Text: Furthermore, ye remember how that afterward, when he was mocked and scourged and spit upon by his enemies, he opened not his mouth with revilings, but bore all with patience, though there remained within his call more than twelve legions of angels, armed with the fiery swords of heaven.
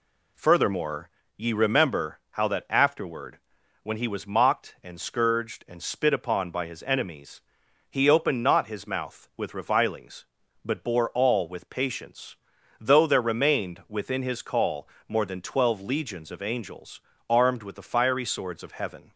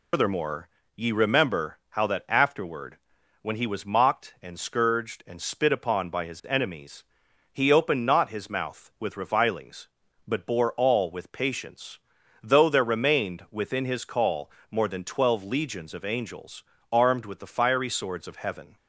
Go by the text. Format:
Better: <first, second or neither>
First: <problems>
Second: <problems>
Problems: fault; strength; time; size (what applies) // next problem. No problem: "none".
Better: first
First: pauses between "call" and "more"; slight; at 14.8 s; 0.22 s long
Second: loses the start of "Furthermore"; at 0.1 s; 185 ms // pauses between "call" and "more"; slight; at 14.4 s; 0.22 s long